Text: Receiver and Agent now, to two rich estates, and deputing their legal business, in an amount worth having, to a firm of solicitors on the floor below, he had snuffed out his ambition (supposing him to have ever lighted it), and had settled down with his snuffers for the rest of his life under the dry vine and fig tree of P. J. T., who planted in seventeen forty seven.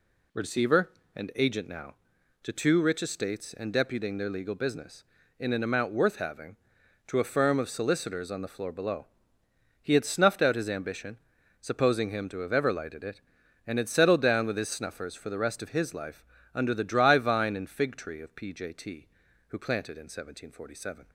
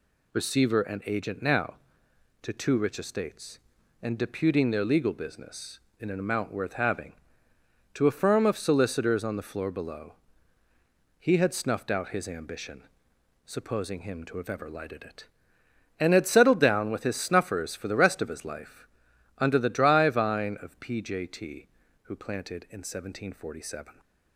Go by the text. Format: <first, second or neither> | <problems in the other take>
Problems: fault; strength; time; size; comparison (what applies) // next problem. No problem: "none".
first | pauses between "life" and "under"; noticeable; at 18.8 s; 0.52 s long; slight in the first // skips "and fig tree"; at 20.5 s